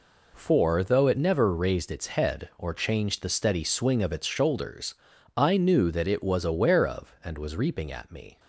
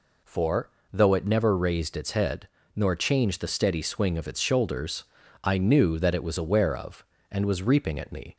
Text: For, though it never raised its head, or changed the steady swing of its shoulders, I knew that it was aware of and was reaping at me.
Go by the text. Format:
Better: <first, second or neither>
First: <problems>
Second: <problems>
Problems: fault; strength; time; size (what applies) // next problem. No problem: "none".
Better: first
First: none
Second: says "nor" for "or"; at 2.7 s